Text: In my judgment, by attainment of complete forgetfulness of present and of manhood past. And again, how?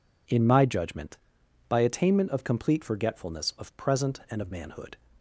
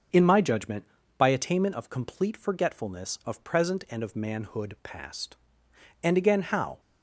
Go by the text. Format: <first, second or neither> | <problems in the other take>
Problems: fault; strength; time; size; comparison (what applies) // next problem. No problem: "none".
second | stops before "past And again how"; at 5.1 s